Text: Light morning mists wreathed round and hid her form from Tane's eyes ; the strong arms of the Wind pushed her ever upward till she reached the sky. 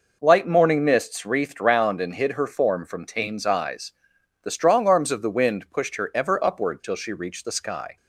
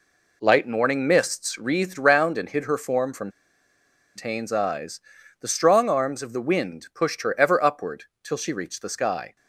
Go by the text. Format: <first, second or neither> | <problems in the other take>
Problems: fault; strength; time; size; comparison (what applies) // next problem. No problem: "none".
first | pauses between "from" and "Tane's"; noticeable; at 3.2 s; 0.86 s long // pauses between "upward" and "till"; slight; at 8.0 s; 0.20 s long